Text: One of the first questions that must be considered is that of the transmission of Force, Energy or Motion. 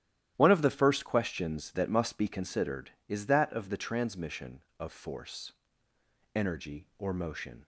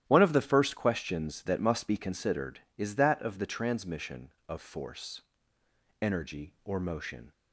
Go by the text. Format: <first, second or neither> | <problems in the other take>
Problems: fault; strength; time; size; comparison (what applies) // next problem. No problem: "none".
neither | starts louder than the rest; strong; the same in both